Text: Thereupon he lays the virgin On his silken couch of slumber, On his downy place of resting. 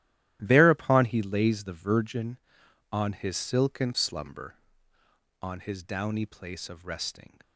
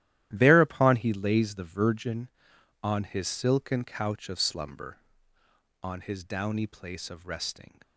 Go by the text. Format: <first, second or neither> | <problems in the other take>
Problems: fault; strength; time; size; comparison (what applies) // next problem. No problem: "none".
second | starts louder than the rest; strong; until 1.4 s; 13 dB; strong in the second // skips "couch of"; at 3.9 s